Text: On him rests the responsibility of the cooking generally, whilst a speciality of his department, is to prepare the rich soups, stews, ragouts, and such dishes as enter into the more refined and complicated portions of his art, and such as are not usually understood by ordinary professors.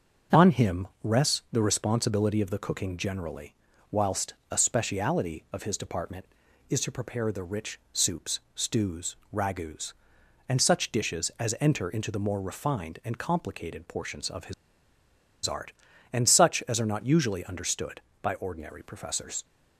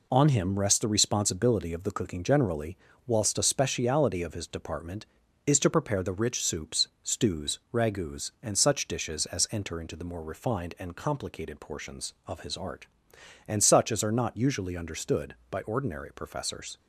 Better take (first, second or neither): second